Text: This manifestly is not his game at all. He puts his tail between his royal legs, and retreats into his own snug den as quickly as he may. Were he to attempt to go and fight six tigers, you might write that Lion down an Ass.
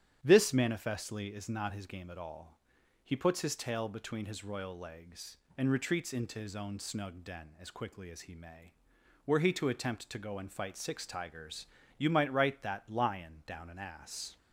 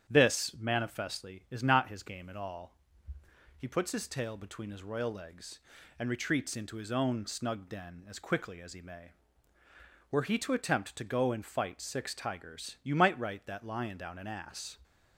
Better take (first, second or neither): neither